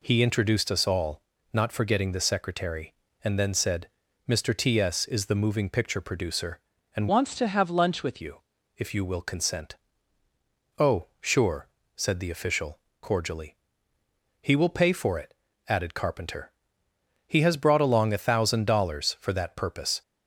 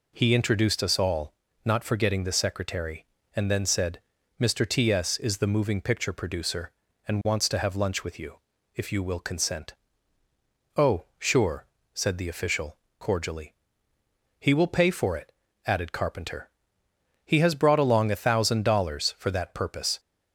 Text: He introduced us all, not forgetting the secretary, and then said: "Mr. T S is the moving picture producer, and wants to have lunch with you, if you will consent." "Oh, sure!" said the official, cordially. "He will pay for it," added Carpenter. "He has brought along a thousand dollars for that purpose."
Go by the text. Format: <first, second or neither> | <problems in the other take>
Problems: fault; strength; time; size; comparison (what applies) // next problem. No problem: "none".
second | changes voice from "wants" to "with"; from 7.0 to 8.2 s; 1.2 s long